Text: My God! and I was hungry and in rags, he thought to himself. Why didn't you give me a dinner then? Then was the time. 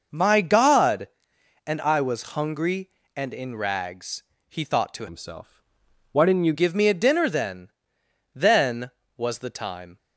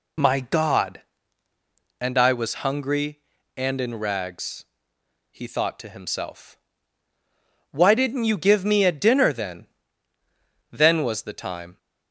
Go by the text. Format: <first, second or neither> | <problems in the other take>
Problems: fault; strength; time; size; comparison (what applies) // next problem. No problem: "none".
second | changes voice from "himself" to "you"; from 5.0 to 6.5 s; 1.5 s long